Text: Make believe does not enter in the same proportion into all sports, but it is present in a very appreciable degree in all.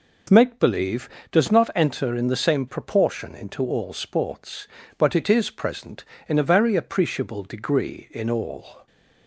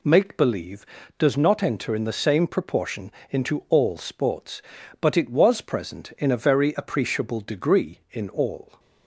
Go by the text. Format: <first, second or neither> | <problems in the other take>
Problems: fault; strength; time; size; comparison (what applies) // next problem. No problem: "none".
first | pauses between "proportion" and "into"; slight; at 3.1 s; 0.18 s long // says "was" for "is"; at 5.2 s